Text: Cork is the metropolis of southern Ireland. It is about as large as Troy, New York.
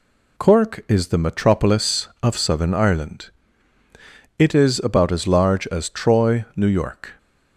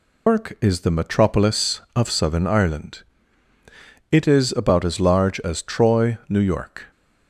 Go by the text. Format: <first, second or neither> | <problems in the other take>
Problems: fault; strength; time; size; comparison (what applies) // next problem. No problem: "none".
first | loses the start of "Cork"; at 0.2 s; 160 ms